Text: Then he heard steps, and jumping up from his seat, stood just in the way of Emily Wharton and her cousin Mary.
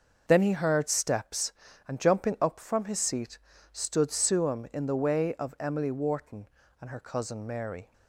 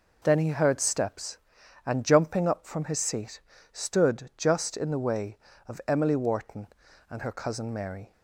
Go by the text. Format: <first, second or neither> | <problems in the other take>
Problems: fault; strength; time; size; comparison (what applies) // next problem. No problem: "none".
second | starts louder than the rest; until 1.2 s; 6.5 dB // says "suam" for "just"; at 4.1 s